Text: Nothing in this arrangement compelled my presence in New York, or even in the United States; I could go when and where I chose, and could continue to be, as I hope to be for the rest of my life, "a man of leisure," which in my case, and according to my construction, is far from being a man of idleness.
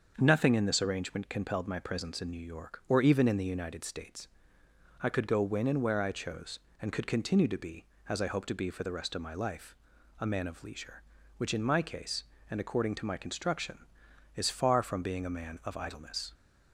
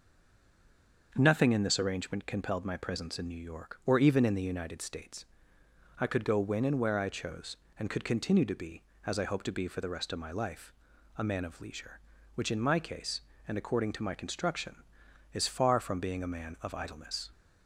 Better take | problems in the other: first | stays silent before the first word; until 1.1 s; 1.1 s long // starts louder than the rest; until 2.1 s; 6.5 dB; also in the first

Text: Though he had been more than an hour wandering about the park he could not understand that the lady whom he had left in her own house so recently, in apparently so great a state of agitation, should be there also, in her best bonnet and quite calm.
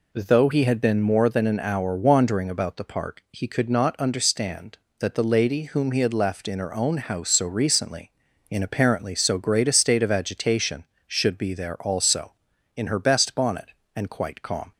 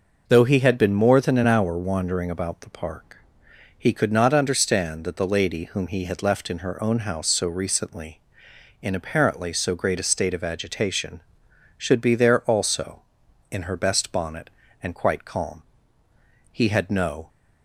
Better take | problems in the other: first | pauses between "park" and "he"; noticeable; at 3.0 s; 0.74 s long // goes on to say "He had no"; noticeable; from 16.5 s on; 0.78 s long

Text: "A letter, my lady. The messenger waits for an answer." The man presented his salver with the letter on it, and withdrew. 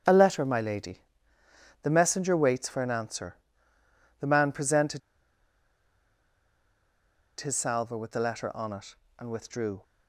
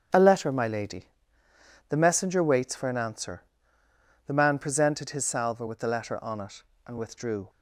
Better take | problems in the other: second | starts louder than the rest; until 1.8 s; 7 dB; also in the second // pauses between "presented" and "his"; strong; at 5.0 s; 2.4 s long

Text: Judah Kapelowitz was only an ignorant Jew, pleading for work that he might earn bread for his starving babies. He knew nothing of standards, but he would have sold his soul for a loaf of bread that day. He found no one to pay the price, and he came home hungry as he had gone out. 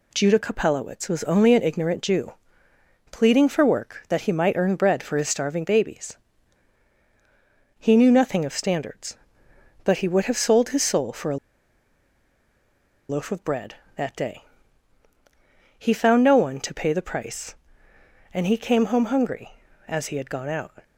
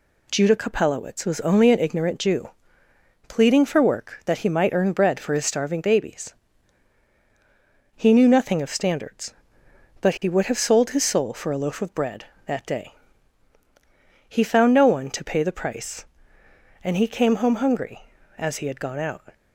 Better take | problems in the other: second | pauses between "a" and "loaf"; strong; at 11.3 s; 1.7 s long

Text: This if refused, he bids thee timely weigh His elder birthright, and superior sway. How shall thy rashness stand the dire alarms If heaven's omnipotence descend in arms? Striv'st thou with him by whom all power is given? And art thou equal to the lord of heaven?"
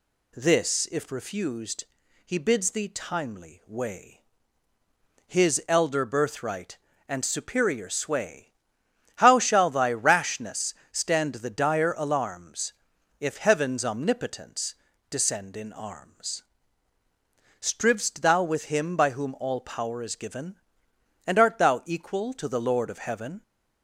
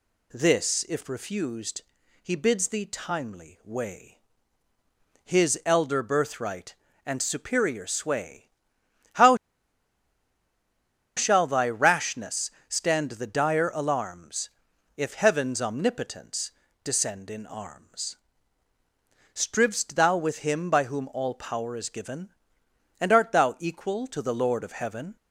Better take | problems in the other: first | pauses between "weigh" and "His"; at 4.2 s; 1.0 s long; also in the first // pauses between "How" and "shall"; strong; at 9.3 s; 1.8 s long // pauses between "rashness" and "stand"; slight; at 12.4 s; 0.18 s long; slight in the first // pauses between "alarms" and "If"; noticeable; at 14.4 s; 0.46 s long; noticeable in the first // pauses between "omnipotence" and "descend"; slight; at 16.4 s; 0.32 s long; slight in the first

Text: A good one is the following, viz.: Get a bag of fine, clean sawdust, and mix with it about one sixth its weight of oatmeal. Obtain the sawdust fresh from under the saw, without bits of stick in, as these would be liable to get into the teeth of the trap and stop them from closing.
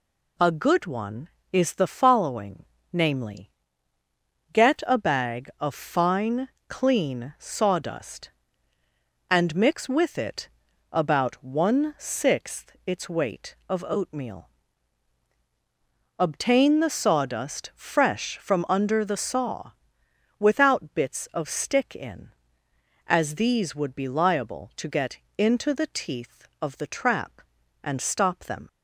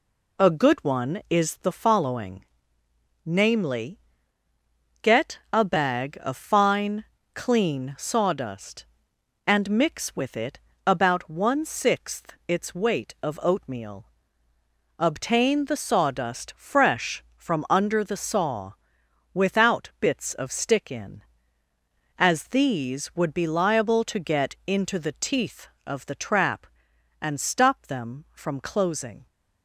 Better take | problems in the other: second | pauses between "it" and "about"; at 10.4 s; 0.44 s long; slight in the second // pauses between "get" and "into"; slight; at 25.1 s; 0.22 s long // stops before "from closing"; at 28.6 s

